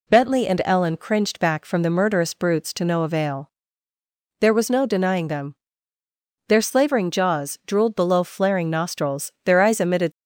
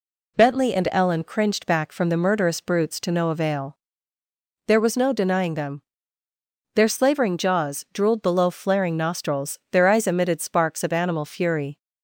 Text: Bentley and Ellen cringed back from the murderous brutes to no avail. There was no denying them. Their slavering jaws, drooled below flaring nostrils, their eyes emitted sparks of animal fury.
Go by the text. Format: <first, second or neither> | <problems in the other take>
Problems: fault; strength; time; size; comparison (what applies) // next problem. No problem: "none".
second | stops before "sparks of animal fury"; at 10.1 s